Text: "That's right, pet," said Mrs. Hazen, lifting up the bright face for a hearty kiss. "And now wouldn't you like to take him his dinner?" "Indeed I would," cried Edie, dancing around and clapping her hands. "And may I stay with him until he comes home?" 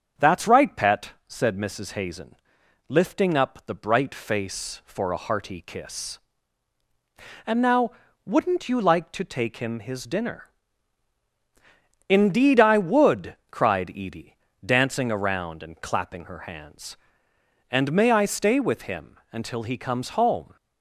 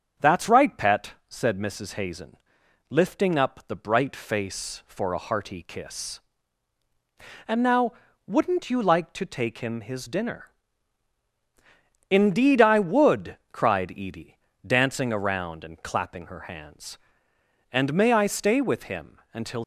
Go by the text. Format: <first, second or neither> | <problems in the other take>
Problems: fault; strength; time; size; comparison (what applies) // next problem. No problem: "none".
first | starts louder than the rest; until 1.3 s; 7 dB; also in the first // pauses between "now" and "wouldn't"; slight; at 7.9 s; 0.34 s long; slight in the first // stops before "he comes home"; at 19.6 s